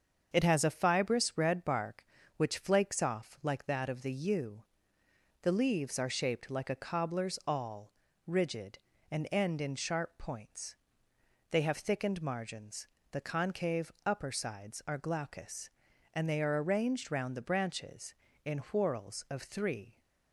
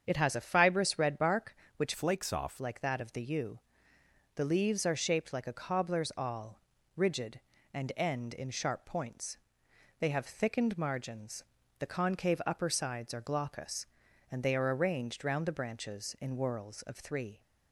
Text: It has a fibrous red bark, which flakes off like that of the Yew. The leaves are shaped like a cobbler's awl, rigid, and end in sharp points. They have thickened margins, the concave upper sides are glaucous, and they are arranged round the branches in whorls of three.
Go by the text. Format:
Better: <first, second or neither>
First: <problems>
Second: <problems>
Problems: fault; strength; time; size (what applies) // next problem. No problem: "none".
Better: first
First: starts louder than the rest; until 1.3 s; 7 dB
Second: starts louder than the rest; strong; until 1.0 s; 7.5 dB // changes voice from "flakes" to "off"; from 1.9 to 2.6 s; 0.7 s long